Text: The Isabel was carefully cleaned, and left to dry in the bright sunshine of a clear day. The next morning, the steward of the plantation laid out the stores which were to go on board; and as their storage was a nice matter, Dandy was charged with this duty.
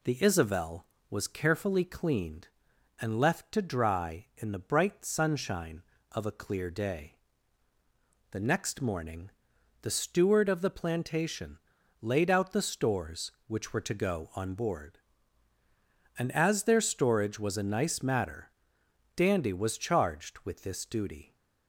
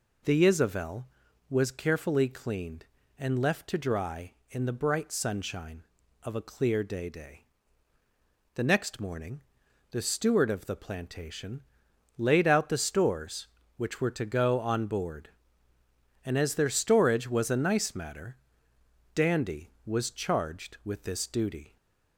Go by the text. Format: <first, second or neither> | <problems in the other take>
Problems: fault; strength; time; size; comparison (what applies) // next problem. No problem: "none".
first | says "day" twice; at 7.0 s // pauses between "plantation" and "laid"; noticeable; at 11.6 s; 0.56 s long; also in the first